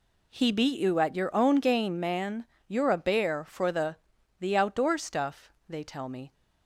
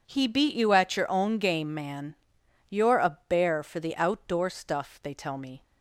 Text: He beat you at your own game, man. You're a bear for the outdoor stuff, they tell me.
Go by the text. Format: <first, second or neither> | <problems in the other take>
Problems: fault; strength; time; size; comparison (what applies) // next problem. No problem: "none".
second | says "the" twice; at 4.4 s